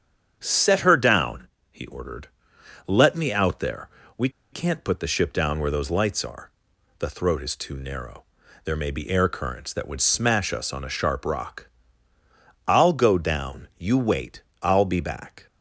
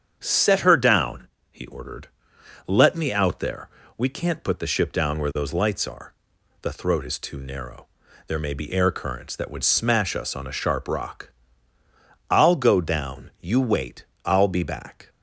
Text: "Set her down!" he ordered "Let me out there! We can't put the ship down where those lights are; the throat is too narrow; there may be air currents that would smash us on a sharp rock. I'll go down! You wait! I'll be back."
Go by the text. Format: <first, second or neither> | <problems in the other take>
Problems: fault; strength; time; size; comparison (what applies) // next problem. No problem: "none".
second | starts louder than the rest; strong; until 1.4 s; 8 dB; strong in the second // pauses between "ordered" and "Let"; noticeable; at 2.2 s; 0.60 s long; noticeable in the second // pauses between "We" and "can't"; slight; at 4.2 s; 0.22 s long